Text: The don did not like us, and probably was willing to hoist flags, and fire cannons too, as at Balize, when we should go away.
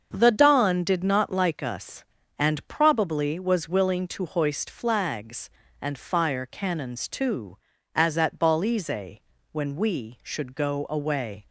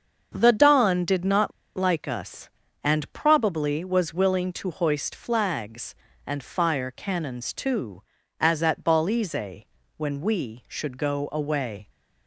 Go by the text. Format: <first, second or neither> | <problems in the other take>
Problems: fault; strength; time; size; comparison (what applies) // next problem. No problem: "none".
first | starts louder than the rest; until 1.3 s; 6.5 dB; also in the first // pauses between "not" and "like"; slight; at 1.5 s; 0.25 s long